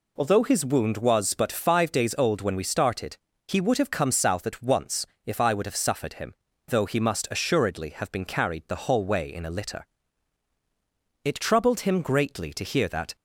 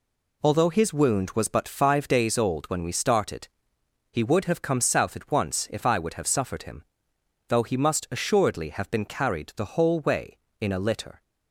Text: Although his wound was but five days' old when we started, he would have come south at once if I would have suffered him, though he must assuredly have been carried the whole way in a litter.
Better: second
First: pauses between "once" and "if"; slight; at 5.0 s; 0.20 s long // goes on to say "It troubled him greatly to hear that"; strong; from 11.2 s on; 1.9 s long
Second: none

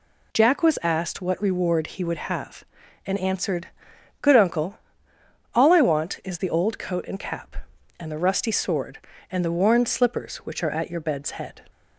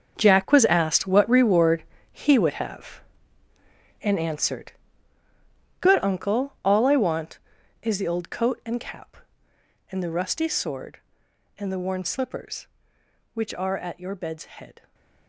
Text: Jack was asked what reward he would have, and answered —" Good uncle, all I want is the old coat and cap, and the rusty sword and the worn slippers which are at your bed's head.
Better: first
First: none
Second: gets quieter; strong; throughout; 13.5 dB // pauses between "reward" and "he"; slight; at 1.8 s; 0.28 s long // stays silent after the last word; slight; from 14.7 s on; 0.5 s long

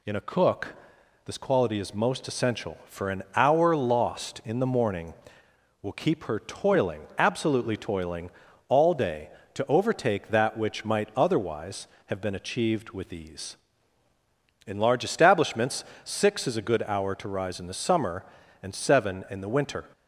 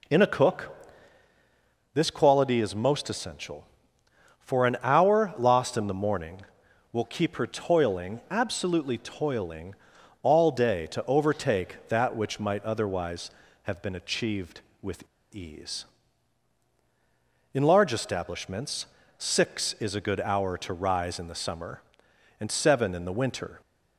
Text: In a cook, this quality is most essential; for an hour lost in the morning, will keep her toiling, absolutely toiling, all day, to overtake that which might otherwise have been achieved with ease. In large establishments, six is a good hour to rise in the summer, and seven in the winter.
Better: first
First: none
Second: pauses between "with" and "ease"; slight; at 15.0 s; 0.27 s long

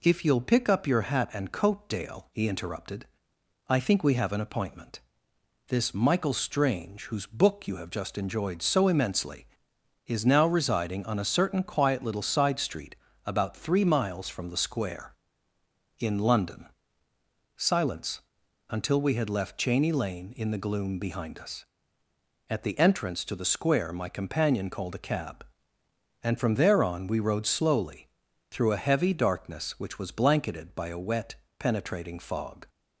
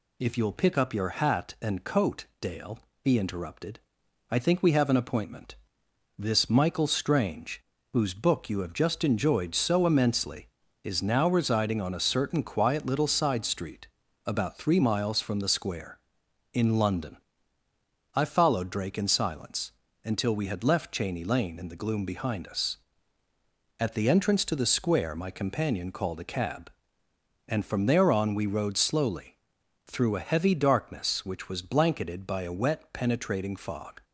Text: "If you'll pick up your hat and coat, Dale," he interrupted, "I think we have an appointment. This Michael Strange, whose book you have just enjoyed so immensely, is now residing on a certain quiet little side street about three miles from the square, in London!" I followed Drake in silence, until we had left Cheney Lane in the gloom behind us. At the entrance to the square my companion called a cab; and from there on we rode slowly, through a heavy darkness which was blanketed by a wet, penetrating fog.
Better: second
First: pauses between "street" and "about"; slight; at 12.9 s; 0.30 s long // skips "I followed Drake in"; at 17.1 s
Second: pauses between "street" and "about"; at 13.8 s; 0.38 s long

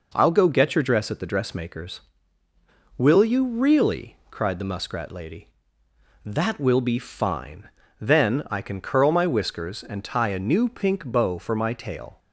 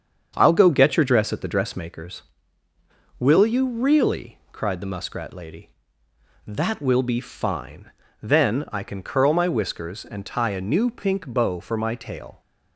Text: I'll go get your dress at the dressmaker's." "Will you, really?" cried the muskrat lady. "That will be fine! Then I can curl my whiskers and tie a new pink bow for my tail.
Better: first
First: none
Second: starts louder than the rest; strong; until 1.9 s; 7 dB

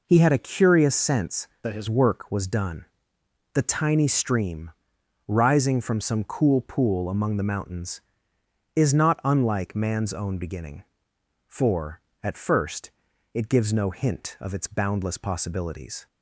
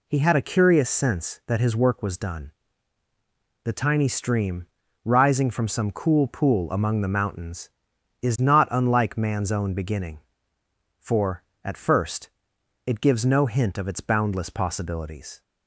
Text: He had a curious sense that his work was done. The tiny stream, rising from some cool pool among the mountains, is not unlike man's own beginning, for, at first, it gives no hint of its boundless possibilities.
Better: second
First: changes voice from "that" to "his"; from 1.6 to 1.8 s; 0.2 s long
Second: none

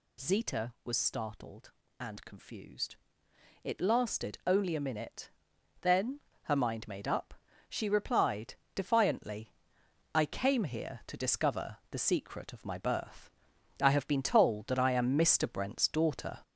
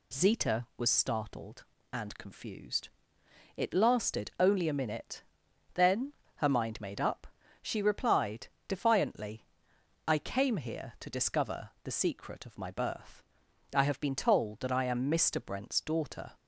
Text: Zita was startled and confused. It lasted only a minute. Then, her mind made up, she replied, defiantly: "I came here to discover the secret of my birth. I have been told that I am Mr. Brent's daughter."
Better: second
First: gets louder; noticeable; throughout; 6 dB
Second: none

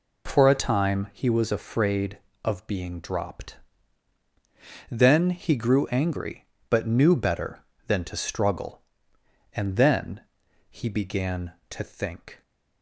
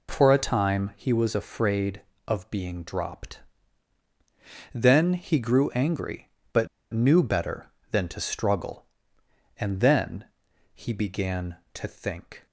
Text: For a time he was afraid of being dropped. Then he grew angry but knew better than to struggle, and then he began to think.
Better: first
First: pauses between "then" and "he"; noticeable; at 10.2 s; 0.48 s long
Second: pauses between "but" and "knew"; slight; at 6.6 s; 0.25 s long // pauses between "then" and "he"; noticeable; at 10.2 s; 0.48 s long

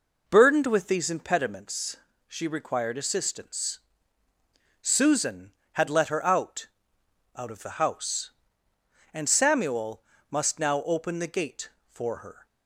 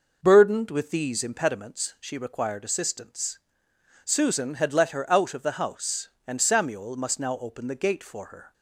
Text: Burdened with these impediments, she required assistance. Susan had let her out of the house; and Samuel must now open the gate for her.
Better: second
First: says "out" twice; at 7.3 s // pauses between "Samuel" and "must"; slight; at 10.0 s; 0.26 s long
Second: none

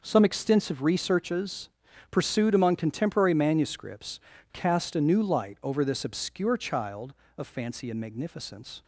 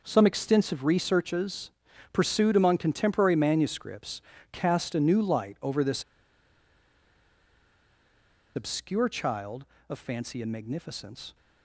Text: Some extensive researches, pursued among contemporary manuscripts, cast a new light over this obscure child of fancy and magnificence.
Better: first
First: none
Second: pauses between "this" and "obscure"; strong; at 6.0 s; 2.5 s long

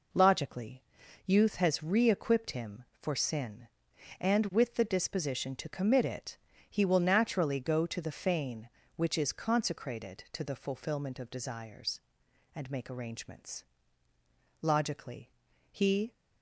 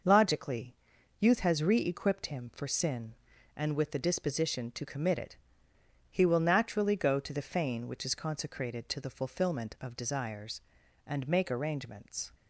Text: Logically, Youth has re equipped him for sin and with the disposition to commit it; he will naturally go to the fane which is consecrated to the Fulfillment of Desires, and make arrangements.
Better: second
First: goes on to say "Logically he"; from 14.6 s on; 1.5 s long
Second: none

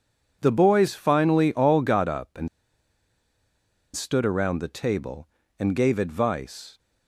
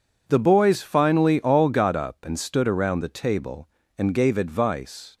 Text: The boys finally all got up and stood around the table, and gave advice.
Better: second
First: pauses between "and" and "stood"; strong; at 2.4 s; 1.4 s long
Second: none

